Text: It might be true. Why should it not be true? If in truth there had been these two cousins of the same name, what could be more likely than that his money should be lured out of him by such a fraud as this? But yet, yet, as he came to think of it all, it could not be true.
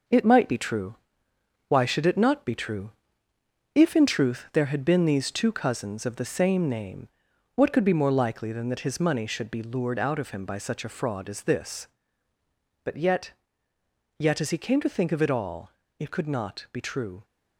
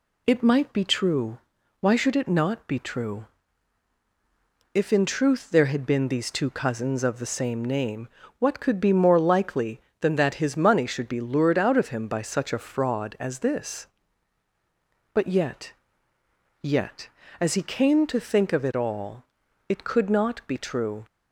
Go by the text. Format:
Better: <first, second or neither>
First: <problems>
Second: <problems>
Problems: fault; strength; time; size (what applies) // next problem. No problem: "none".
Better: second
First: gets quieter; throughout; 6.5 dB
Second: none